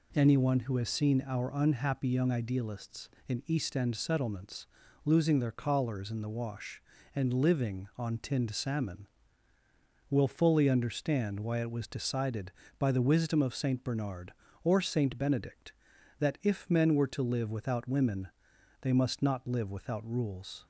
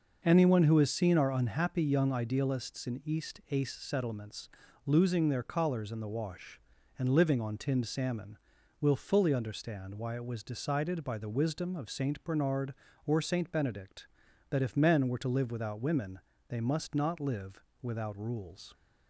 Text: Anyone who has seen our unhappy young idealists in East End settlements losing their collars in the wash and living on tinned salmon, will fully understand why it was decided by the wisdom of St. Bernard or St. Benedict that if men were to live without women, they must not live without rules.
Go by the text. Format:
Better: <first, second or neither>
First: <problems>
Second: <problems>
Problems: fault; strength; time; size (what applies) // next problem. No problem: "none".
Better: first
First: pauses between "settlements" and "losing"; at 4.6 s; 0.40 s long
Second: says "Ace" for "End"; at 3.5 s // pauses between "settlements" and "losing"; slight; at 4.4 s; 0.36 s long // pauses between "live" and "without"; slight; at 17.6 s; 0.20 s long